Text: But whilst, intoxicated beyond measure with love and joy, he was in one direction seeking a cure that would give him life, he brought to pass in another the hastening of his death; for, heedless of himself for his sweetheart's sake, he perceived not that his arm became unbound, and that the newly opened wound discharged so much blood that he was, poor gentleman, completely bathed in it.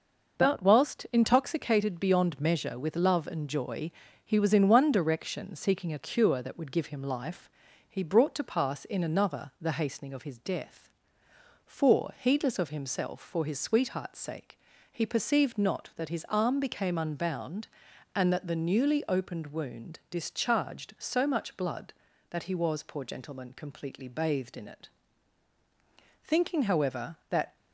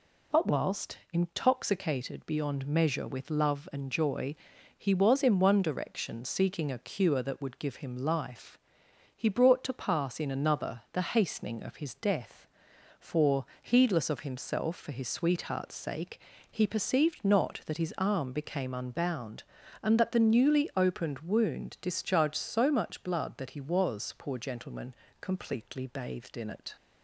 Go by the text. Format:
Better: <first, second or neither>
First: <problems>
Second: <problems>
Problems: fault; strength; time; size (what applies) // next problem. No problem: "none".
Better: second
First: goes on to say "Thinking however that"; from 26.2 s on; 1.3 s long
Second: none